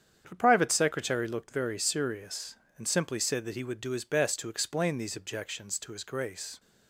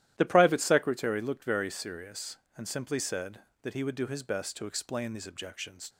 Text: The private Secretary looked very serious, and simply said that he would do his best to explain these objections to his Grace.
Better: first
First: starts louder than the rest; strong; until 1.2 s; 8.5 dB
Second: starts louder than the rest; strong; until 1.1 s; 12.5 dB // stops before "to his Grace"; at 5.8 s

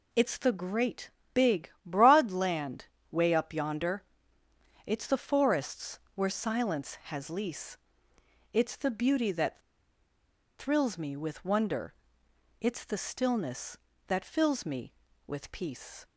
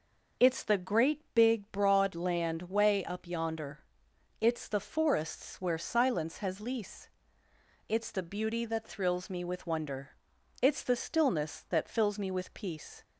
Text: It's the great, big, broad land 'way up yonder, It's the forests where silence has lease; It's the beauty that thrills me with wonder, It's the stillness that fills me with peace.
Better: second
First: pauses between "land" and "way"; slight; at 2.8 s; 0.24 s long // pauses between "forests" and "where"; slight; at 5.9 s; 0.16 s long // pauses between "that" and "thrills"; at 9.6 s; 0.98 s long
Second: none

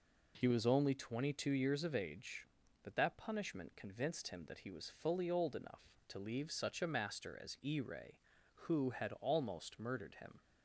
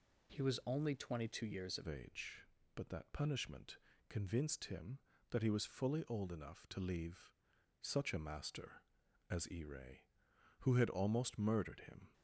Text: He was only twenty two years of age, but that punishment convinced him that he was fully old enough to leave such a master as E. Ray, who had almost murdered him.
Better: first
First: none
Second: changes voice at "age"; from 1.8 s on; 10.3 s long // pauses between "punishment" and "convinced"; slight; at 3.7 s; 0.32 s long // pauses between "leave" and "such"; noticeable; at 7.3 s; 0.46 s long

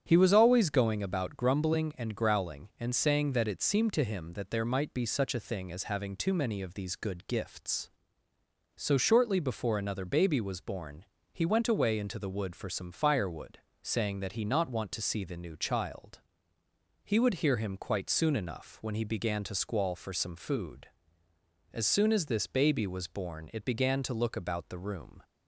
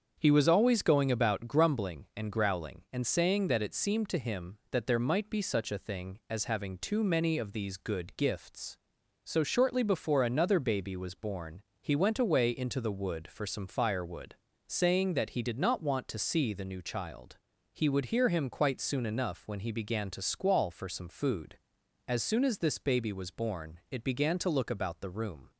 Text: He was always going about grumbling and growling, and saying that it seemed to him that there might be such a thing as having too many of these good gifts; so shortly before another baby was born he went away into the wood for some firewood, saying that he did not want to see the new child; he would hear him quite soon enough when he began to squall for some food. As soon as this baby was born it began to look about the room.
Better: second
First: starts louder than the rest; strong; until 1.0 s; 9 dB // pauses between "born" and "he"; slight; at 11.0 s; 0.30 s long // skips "did"; at 14.4 s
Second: starts louder than the rest; strong; until 1.1 s; 7 dB // pauses between "born" and "he"; slight; at 11.6 s; 0.18 s long

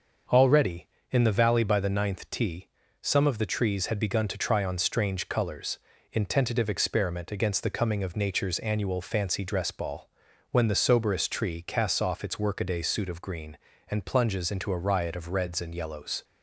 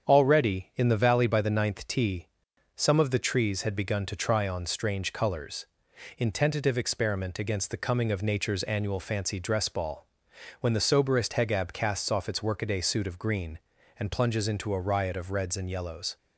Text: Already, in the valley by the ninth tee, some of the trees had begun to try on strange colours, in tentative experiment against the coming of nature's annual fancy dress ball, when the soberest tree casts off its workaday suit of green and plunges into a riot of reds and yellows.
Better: first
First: starts louder than the rest; until 1.5 s; 6.5 dB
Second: starts louder than the rest; strong; until 1.1 s; 7.5 dB // says "hegab" for "tree"; at 11.3 s

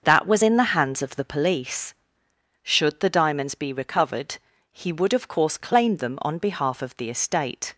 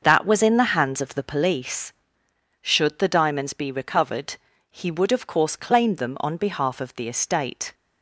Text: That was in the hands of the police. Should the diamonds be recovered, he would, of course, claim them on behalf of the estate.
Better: neither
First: starts louder than the rest; until 1.0 s; 6.5 dB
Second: starts louder than the rest; until 1.0 s; 6.5 dB

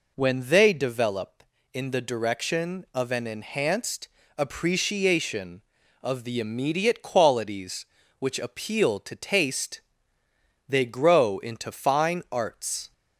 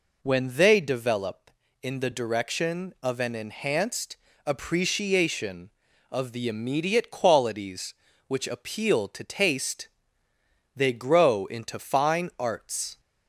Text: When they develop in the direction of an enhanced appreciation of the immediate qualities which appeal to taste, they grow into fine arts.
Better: neither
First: pauses between "enhanced" and "appreciation"; slight; at 4.0 s; 0.28 s long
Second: pauses between "enhanced" and "appreciation"; slight; at 4.1 s; 0.28 s long

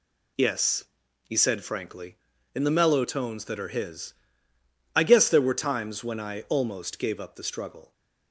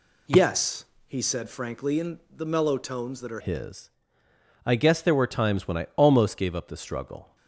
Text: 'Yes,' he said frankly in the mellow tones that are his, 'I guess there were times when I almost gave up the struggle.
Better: first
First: none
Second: changes voice at "his"; from 3.3 s on; 4.0 s long

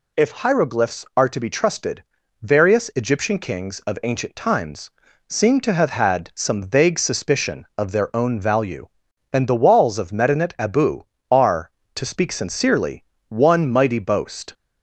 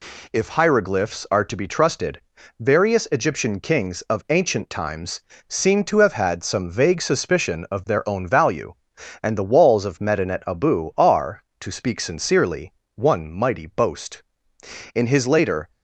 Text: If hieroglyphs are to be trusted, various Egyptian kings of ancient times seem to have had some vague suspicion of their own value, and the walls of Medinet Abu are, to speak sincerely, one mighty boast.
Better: first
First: pauses between "times" and "seem"; slight; at 4.9 s; 0.36 s long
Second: pauses between "times" and "seem"; slight; at 5.2 s; 0.28 s long // goes on to say "In his later"; noticeable; from 14.9 s on; 0.78 s long

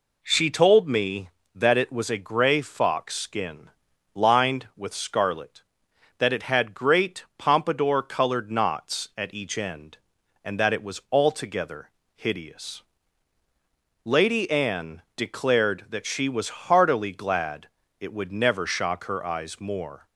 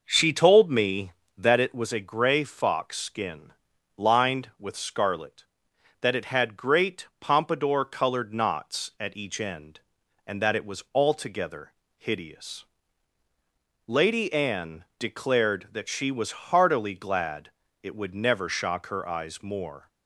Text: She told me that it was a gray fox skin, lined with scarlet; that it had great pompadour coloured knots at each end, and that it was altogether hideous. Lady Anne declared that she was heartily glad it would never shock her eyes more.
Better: first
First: pauses between "altogether" and "hideous"; slight; at 11.8 s; 0.24 s long // pauses between "glad" and "it"; slight; at 17.6 s; 0.32 s long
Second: starts louder than the rest; noticeable; until 1.7 s; 5.5 dB // pauses between "altogether" and "hideous"; slight; at 11.7 s; 0.24 s long // pauses between "glad" and "it"; slight; at 17.4 s; 0.32 s long

